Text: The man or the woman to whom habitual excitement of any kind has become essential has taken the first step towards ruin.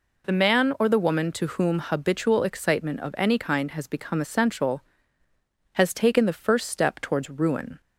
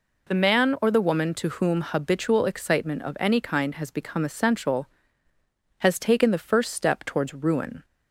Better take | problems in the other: neither | none

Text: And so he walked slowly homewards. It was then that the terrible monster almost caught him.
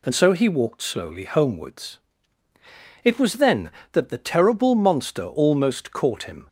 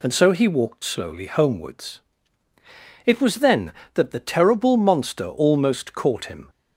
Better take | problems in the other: neither | none

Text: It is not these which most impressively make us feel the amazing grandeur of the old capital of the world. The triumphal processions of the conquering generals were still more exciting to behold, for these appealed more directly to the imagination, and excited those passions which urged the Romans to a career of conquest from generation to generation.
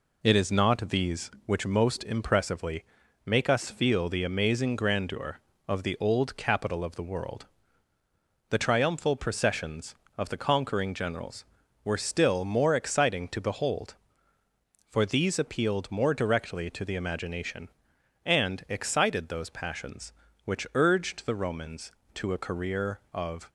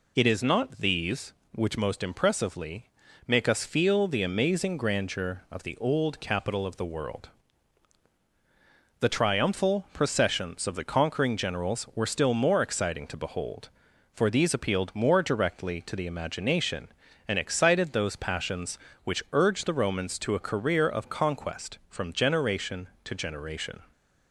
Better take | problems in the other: second | pauses between "impressively" and "make"; at 2.8 s; 0.42 s long; also in the second // stops before "conquest from generation to generation"; at 23.4 s

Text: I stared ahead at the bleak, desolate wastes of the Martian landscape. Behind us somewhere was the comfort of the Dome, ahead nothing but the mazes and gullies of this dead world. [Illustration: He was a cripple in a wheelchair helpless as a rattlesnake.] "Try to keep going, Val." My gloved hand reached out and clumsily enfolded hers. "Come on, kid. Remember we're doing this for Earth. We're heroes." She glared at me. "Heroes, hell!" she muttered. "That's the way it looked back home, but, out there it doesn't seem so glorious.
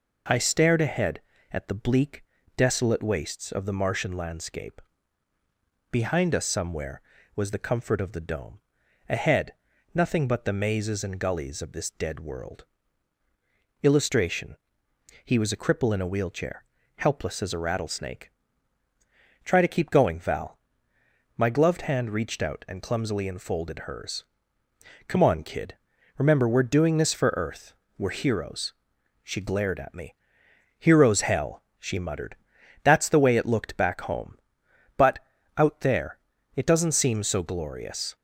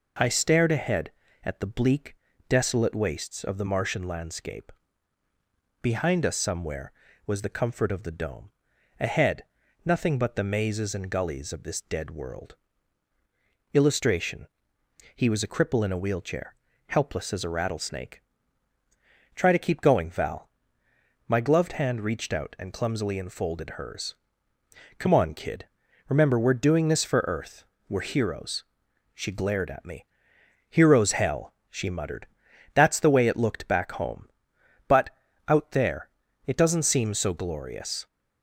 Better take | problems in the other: neither | pauses between "ahead" and "nothing"; the same in both // pauses between "wheelchair" and "helpless"; slight; the same in both // pauses between "there" and "it"; slight; the same in both

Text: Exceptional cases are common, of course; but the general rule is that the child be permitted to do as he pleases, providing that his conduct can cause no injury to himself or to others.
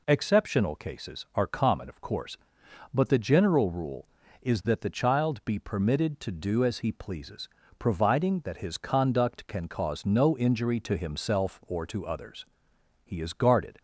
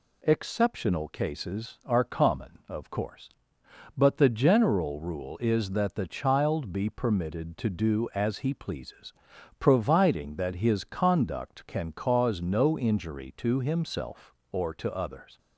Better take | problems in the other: second | goes on to say "He is guarded"; noticeable; from 13.0 s on; 0.76 s long

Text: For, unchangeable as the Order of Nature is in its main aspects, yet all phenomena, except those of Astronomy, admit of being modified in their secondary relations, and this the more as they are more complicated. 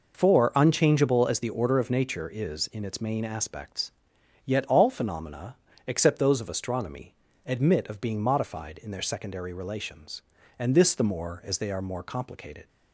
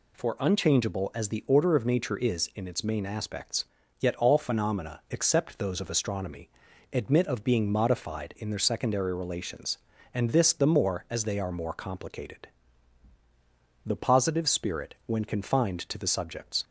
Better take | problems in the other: first | goes on to say "The Positive spirit when confined to the subjects"; strong; from 13.8 s on; 2.7 s long

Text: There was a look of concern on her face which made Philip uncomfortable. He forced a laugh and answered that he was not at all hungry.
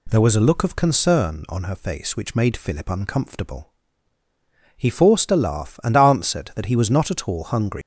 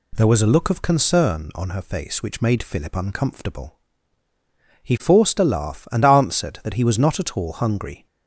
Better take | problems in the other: second | leaves "hungry" unfinished; at 7.8 s; 155 ms

